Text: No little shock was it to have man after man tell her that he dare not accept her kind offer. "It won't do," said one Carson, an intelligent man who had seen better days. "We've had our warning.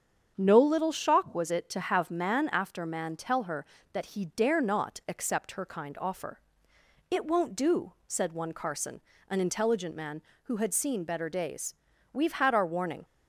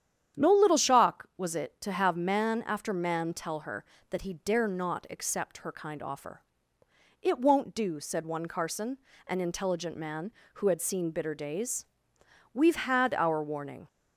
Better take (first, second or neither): first